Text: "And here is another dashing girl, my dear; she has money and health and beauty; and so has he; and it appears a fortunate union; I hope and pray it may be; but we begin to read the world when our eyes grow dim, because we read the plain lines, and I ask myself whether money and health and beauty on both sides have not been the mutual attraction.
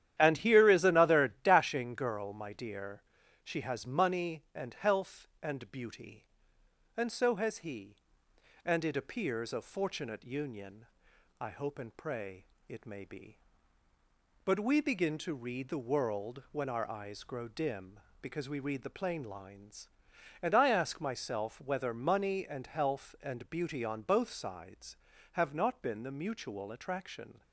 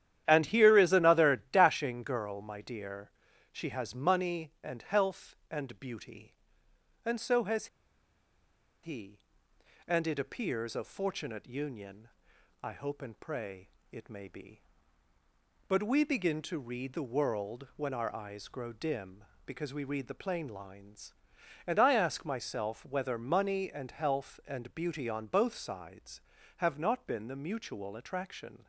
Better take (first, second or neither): first